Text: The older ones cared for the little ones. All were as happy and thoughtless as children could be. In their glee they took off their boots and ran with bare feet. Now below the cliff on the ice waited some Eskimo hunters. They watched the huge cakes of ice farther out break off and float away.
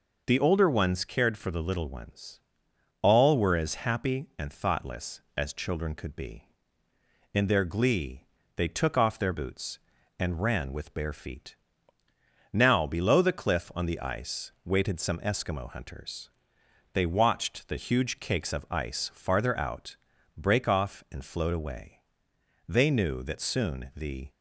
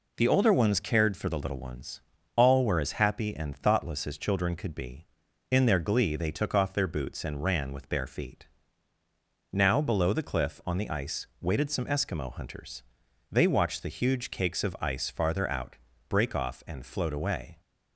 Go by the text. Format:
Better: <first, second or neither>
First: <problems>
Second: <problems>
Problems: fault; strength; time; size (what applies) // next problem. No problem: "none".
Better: second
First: pauses between "glee" and "they"; slight; at 8.2 s; 0.30 s long // pauses between "out" and "break"; at 19.9 s; 0.40 s long // goes on to say "They knew that soon the"; from 22.6 s on; 1.6 s long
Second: pauses between "out" and "break"; slight; at 15.7 s; 0.32 s long